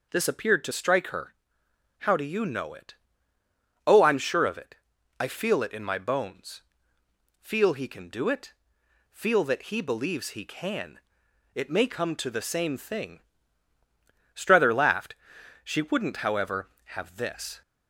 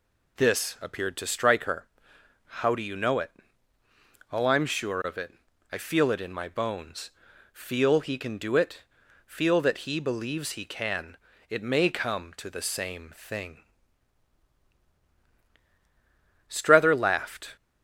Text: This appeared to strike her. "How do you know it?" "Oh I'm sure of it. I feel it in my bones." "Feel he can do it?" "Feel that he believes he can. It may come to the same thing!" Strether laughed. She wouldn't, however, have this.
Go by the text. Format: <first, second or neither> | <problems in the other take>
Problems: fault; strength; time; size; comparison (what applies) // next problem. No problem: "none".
first | stops before "She wouldn't however have this"; at 17.5 s